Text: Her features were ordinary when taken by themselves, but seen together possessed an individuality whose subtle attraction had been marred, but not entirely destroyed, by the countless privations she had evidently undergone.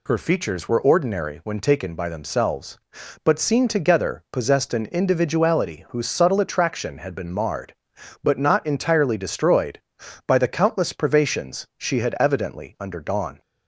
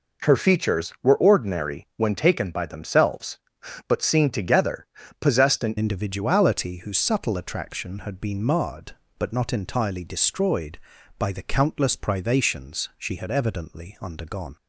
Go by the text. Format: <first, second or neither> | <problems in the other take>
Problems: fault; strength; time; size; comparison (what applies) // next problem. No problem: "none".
first | pauses between "together" and "possessed"; slight; at 4.8 s; 0.36 s long // changes voice at "individuality"; from 5.7 s on; 8.8 s long